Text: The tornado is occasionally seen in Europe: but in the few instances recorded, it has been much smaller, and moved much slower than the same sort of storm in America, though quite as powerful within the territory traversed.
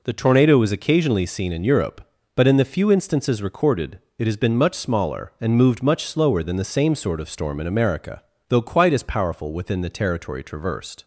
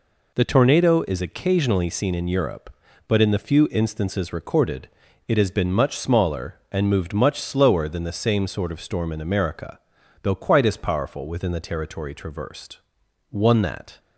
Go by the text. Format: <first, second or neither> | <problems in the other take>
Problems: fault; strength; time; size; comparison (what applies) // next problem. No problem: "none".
first | goes on to say "One that"; noticeable; from 13.2 s on; 0.70 s long